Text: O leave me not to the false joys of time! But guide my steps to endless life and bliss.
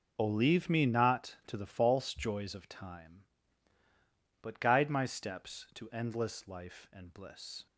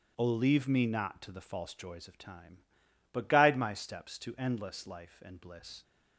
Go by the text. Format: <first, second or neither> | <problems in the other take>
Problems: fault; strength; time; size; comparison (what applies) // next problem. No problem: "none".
neither | none